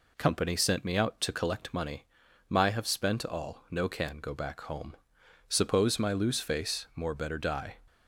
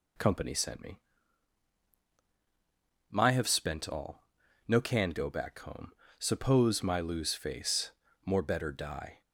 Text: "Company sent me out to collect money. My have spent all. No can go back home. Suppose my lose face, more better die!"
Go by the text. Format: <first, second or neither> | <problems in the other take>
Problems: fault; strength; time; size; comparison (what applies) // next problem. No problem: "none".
first | skips "out to collect money"; at 2.0 s